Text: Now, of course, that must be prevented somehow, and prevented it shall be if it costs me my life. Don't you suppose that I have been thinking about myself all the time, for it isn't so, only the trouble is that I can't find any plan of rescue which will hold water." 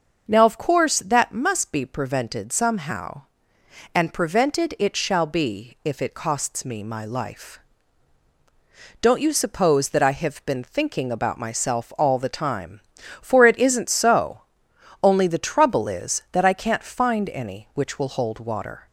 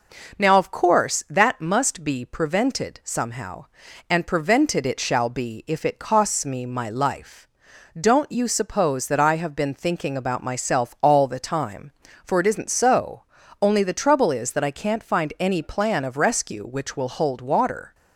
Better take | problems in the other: second | starts louder than the rest; until 1.2 s; 6.5 dB // skips "plan of rescue"; at 17.7 s

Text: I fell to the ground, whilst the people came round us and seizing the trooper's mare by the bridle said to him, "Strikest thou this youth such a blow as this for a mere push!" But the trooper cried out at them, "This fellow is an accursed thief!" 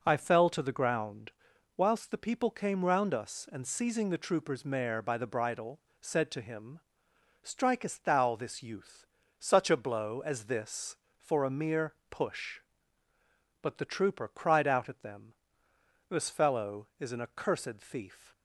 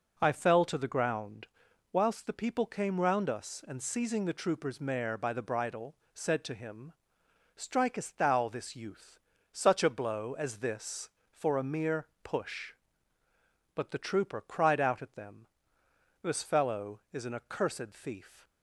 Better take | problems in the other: neither | pauses between "bridle" and "said"; slight; the same in both // pauses between "youth" and "such"; slight; the same in both // pauses between "mere" and "push"; slight; the same in both

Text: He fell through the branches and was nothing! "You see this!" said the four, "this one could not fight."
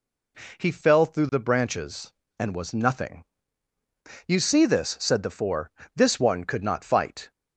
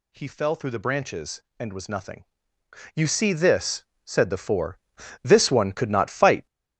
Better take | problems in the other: first | gets louder; strong; throughout; 7 dB

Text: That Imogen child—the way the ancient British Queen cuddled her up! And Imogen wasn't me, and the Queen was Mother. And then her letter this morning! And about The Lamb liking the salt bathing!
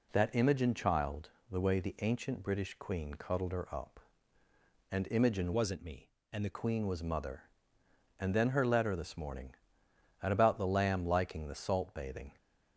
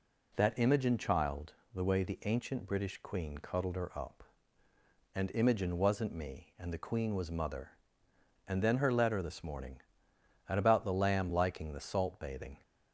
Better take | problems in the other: second | changes voice from "wasn't" to "the"; from 5.5 to 6.5 s; 1.0 s long

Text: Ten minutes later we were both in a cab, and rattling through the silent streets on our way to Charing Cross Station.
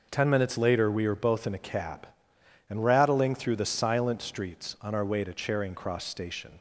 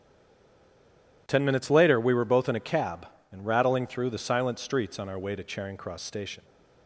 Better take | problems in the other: first | stays silent before the first word; noticeable; until 1.2 s; 1.2 s long

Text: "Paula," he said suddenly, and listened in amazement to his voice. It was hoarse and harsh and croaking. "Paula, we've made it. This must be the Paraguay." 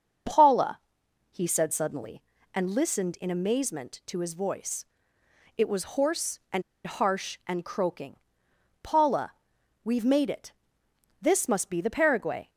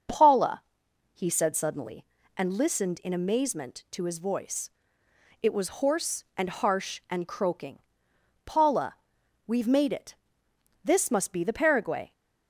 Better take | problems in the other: second | starts louder than the rest; noticeable; until 1.7 s; 6 dB; noticeable in the second // pauses between "and" and "harsh"; slight; at 6.6 s; 0.24 s long

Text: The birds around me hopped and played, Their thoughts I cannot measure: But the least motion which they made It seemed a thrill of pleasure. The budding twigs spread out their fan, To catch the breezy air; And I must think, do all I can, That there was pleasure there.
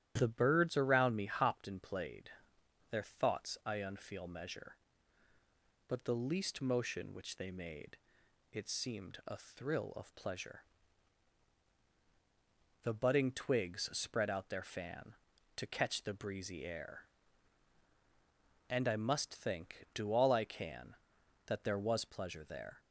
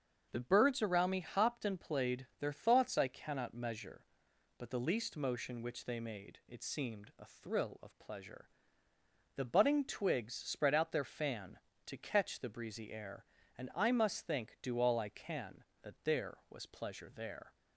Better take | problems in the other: second | starts louder than the rest; strong; until 1.1 s; 11.5 dB; also in the second // says "unfeel" for "cannot"; at 3.8 s // pauses between "made" and "It"; noticeable; at 7.9 s; 0.54 s long

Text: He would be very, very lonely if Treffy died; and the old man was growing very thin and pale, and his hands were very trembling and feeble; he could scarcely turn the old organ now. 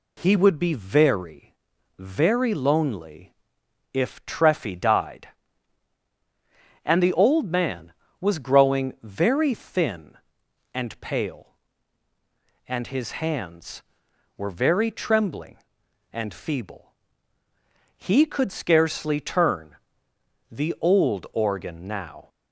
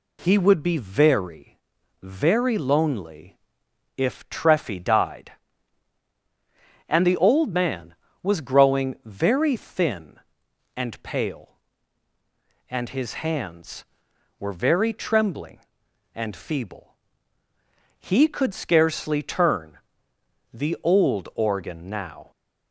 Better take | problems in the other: neither | pauses between "lonely" and "if"; noticeable; the same in both // pauses between "turn" and "the"; noticeable; the same in both

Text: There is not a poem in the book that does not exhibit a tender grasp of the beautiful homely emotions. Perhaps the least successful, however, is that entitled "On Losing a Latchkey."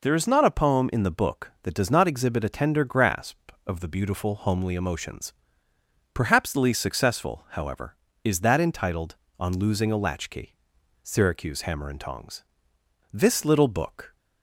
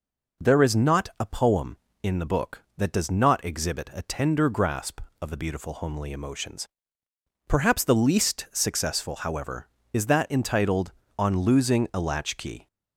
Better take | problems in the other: second | goes on to say "Syracuse Hammer and Tongs This little book"; strong; from 11.0 s on; 3.1 s long

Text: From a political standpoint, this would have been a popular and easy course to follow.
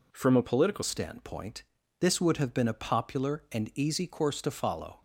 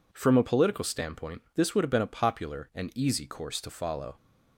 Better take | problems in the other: second | changes voice at "standpoint"; from 0.8 s on; 4.2 s long

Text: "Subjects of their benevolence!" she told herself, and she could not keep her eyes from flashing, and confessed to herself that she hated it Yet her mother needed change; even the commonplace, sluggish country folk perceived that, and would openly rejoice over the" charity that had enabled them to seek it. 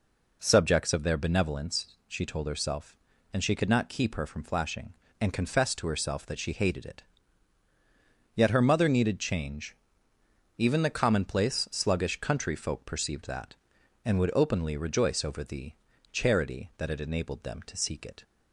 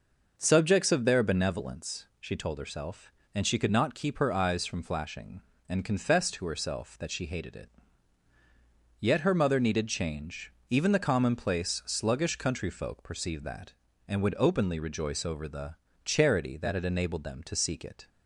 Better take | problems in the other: second | skips "eyes"; at 4.2 s // pauses between "it" and "Yet"; strong; at 7.0 s; 1.3 s long; strong in the second // pauses between "the" and "charity"; at 15.7 s; 0.40 s long; slight in the second

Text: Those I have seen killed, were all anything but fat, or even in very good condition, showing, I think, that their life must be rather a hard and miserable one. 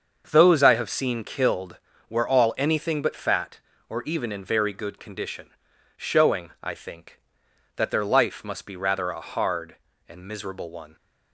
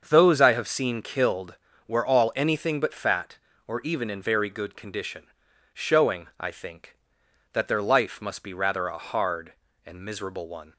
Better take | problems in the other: neither | starts louder than the rest; the same in both

